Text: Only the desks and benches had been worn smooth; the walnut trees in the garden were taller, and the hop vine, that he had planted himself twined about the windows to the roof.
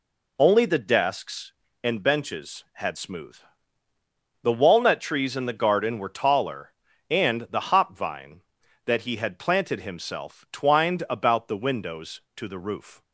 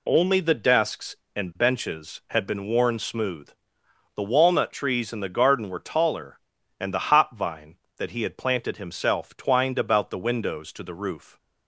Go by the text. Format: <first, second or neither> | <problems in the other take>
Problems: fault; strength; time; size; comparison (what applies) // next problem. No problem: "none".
second | skips "been worn"; at 2.9 s